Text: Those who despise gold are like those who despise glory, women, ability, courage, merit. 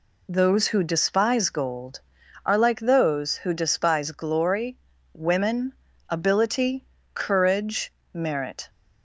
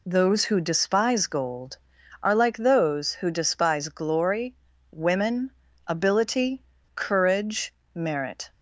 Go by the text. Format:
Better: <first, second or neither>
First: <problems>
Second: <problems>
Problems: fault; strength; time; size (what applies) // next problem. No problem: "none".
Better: neither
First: none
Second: none